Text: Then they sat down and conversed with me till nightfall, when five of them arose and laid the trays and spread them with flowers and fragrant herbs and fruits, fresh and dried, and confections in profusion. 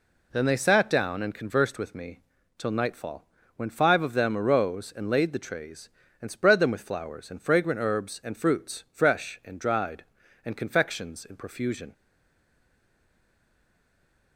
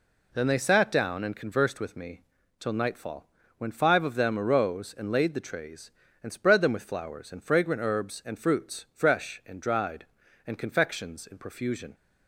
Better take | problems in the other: second | pauses between "me" and "till"; at 2.1 s; 0.38 s long; also in the second // stays silent after the last word; from 11.9 s on; 2.4 s long

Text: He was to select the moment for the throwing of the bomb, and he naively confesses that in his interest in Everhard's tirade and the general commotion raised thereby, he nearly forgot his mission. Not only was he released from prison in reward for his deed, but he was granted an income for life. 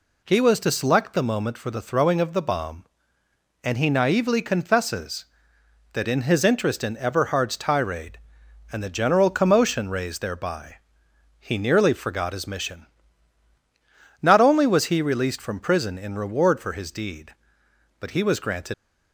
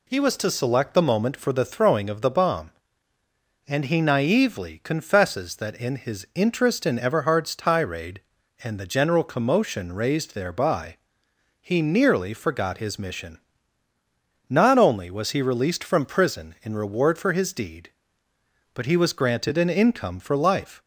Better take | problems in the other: second | stops before "an income for life"; at 18.7 s

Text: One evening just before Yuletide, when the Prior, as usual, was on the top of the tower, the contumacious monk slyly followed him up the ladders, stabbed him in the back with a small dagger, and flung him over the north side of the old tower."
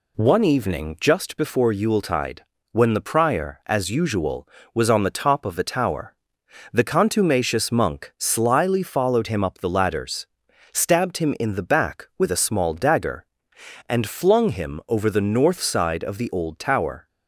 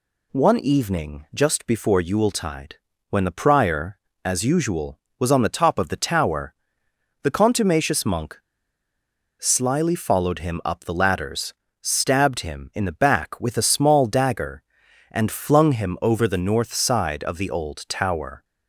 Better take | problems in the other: first | pauses between "monk" and "slyly"; at 8.3 s; 1.0 s long

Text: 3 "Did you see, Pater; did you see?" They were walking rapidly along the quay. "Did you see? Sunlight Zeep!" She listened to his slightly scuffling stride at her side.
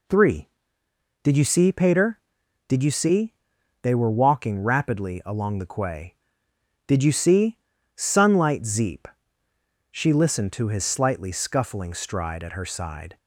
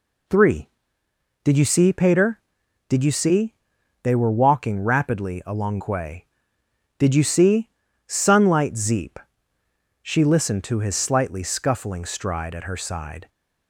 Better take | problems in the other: first | skips "the"; at 5.7 s

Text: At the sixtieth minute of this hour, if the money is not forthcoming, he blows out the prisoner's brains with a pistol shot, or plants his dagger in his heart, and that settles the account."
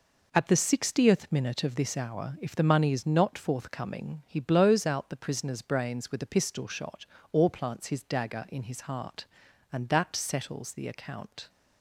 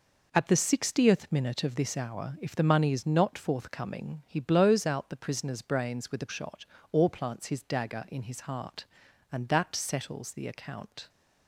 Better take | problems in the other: first | skips "pistol"; at 6.2 s

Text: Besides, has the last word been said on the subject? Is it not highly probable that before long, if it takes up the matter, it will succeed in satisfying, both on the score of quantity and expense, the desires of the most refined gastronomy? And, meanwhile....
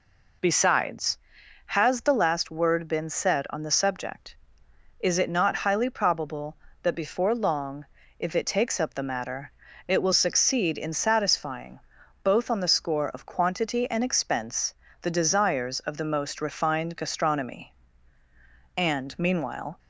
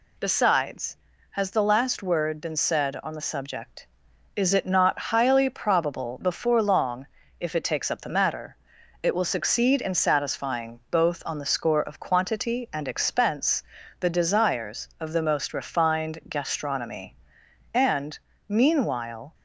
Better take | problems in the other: first | skips "that"; at 6.2 s

